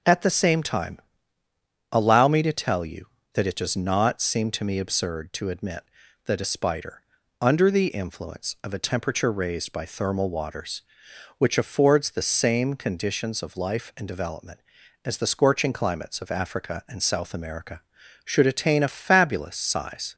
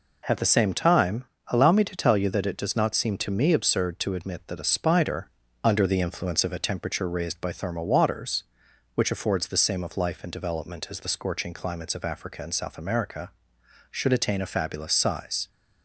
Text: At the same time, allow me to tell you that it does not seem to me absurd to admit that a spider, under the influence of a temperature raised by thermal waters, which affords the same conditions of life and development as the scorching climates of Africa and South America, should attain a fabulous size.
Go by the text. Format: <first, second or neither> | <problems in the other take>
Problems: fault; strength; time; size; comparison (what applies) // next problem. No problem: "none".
first | skips "conditions"; at 9.8 s